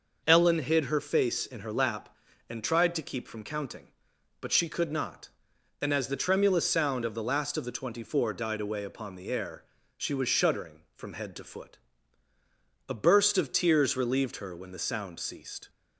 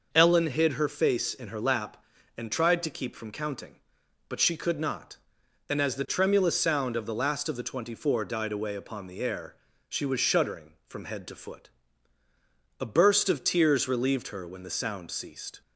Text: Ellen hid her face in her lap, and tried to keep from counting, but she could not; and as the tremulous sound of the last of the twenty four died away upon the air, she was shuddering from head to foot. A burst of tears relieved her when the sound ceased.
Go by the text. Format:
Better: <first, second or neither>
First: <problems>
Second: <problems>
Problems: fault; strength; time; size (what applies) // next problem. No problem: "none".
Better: neither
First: none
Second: none